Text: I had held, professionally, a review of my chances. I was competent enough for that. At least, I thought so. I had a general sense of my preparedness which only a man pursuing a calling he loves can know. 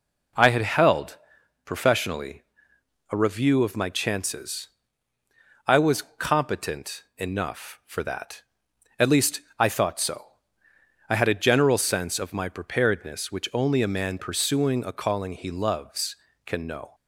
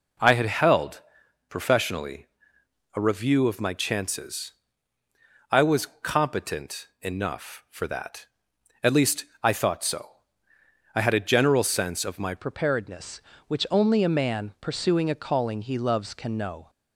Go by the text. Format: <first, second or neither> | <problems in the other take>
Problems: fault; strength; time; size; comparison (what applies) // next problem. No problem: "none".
first | pauses between "was" and "competent"; slight; at 5.8 s; 0.16 s long; slight in the first // changes voice at "preparedness"; from 12.3 s on; 4.3 s long